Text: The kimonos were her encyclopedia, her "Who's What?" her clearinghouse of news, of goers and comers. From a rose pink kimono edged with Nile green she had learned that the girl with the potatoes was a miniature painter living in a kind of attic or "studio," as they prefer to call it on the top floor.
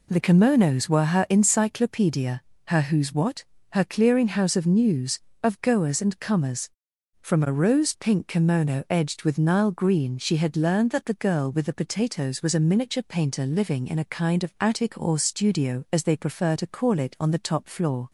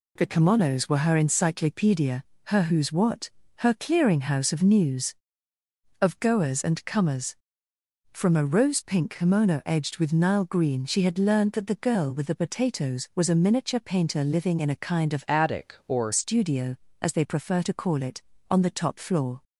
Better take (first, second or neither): first